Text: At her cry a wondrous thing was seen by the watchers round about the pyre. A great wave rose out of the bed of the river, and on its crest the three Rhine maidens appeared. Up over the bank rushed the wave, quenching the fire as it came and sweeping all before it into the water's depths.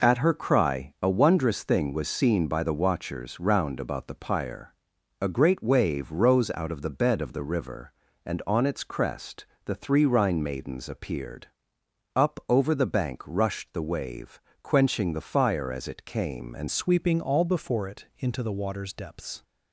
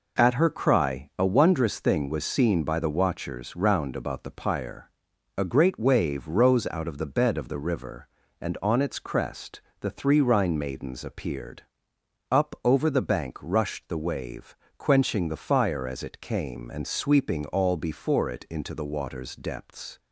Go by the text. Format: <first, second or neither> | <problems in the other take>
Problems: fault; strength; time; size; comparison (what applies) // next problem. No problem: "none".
second | pauses between "crest" and "the"; slight; at 9.4 s; 0.20 s long; slight in the second // changes voice at "sweeping"; from 16.6 s on; 2.8 s long